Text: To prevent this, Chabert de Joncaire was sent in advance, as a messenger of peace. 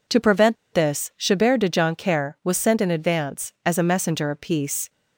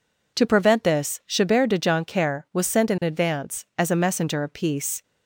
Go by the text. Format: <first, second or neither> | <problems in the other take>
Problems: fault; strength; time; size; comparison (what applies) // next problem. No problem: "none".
second | pauses between "prevent" and "this"; slight; at 0.5 s; 0.17 s long